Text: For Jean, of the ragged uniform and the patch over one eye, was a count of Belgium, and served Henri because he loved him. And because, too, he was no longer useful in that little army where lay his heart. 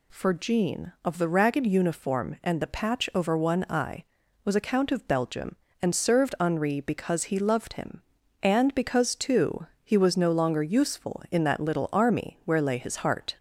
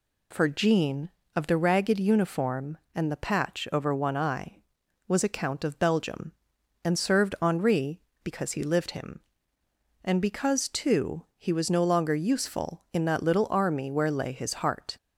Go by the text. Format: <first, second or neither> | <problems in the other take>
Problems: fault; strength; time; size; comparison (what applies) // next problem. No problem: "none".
first | says "lived" for "loved"; at 8.6 s